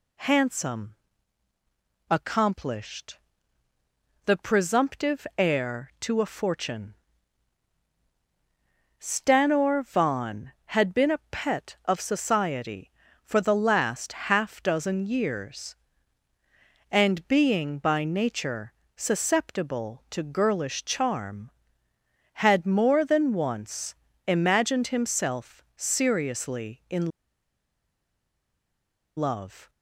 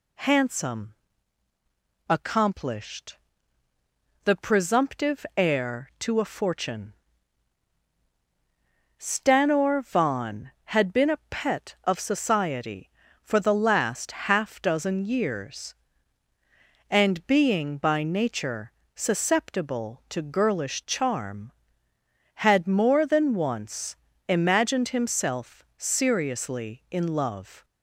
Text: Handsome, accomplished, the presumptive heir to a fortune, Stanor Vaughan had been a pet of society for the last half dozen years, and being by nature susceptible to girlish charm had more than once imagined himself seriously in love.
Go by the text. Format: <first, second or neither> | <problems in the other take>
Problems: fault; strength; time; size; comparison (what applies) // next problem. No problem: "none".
second | pauses between "nature" and "susceptible"; slight; at 18.7 s; 0.22 s long; slight in the second // pauses between "once" and "imagined"; slight; at 23.9 s; 0.32 s long; slight in the second // pauses between "in" and "love"; strong; at 27.1 s; 2.0 s long